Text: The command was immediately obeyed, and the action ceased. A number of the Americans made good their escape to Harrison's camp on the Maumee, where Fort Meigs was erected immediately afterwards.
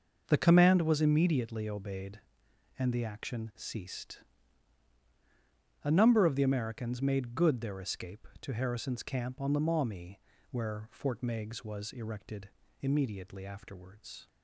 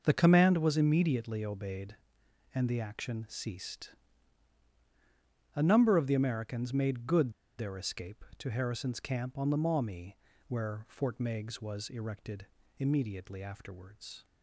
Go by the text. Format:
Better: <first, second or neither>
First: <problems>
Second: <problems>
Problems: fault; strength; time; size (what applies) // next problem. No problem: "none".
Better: first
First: pauses between "erected" and "immediately"; slight; at 12.4 s; 0.30 s long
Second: pauses between "good" and "their"; slight; at 7.3 s; 0.26 s long // pauses between "erected" and "immediately"; slight; at 12.4 s; 0.30 s long